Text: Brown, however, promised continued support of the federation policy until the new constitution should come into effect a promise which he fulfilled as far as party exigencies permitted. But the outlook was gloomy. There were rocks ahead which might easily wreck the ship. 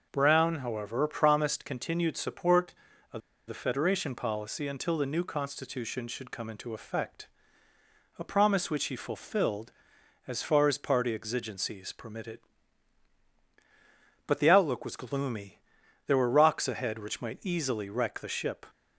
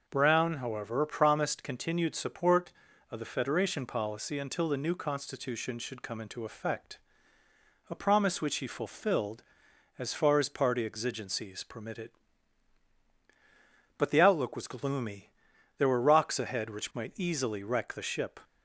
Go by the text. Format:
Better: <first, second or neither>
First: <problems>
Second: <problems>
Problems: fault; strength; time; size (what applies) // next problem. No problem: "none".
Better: second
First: pauses between "of" and "the"; slight; at 3.2 s; 0.27 s long // pauses between "effect" and "a"; noticeable; at 7.2 s; 0.90 s long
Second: pauses between "effect" and "a"; noticeable; at 6.9 s; 0.90 s long